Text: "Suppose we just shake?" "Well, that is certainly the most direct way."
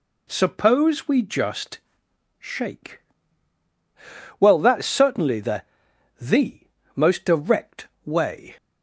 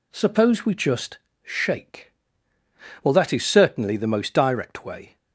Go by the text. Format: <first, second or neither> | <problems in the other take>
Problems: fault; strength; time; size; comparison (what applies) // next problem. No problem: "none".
second | pauses between "just" and "shake"; noticeable; at 1.7 s; 0.61 s long; slight in the second // says "the" twice; at 6.2 s // pauses between "direct" and "way"; slight; at 7.8 s; 0.18 s long